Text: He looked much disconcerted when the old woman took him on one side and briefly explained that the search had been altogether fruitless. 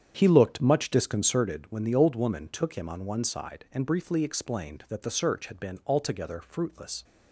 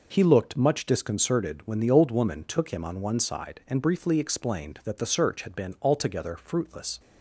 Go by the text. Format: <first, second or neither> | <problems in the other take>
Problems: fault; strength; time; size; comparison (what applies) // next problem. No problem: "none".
second | starts louder than the rest; strong; until 1.6 s; 8.5 dB